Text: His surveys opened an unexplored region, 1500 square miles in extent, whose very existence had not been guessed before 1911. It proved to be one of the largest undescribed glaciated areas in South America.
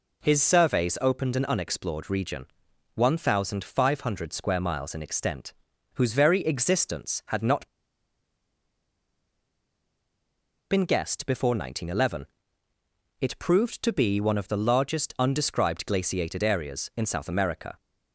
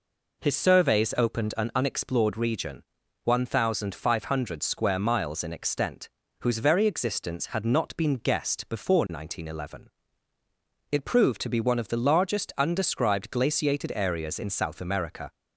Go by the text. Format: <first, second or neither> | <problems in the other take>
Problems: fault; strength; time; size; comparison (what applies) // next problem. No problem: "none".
second | pauses between "not" and "been"; strong; at 7.6 s; 3.0 s long